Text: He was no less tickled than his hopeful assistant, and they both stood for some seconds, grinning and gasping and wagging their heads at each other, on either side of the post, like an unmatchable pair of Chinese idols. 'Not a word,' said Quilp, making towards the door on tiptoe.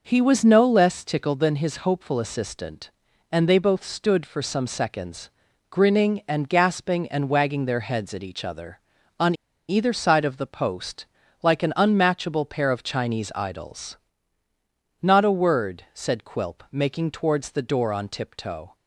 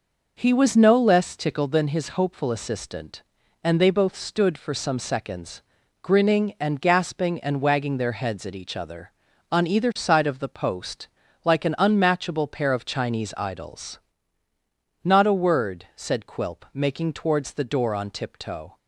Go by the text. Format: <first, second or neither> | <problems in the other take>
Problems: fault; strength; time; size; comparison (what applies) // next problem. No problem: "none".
second | pauses between "on" and "either"; slight; at 9.3 s; 0.35 s long